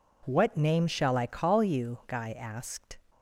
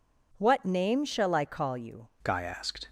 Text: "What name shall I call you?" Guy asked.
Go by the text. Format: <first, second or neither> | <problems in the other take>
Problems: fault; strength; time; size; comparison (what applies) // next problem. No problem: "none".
first | changes voice at "Guy"; from 2.2 s on; 0.6 s long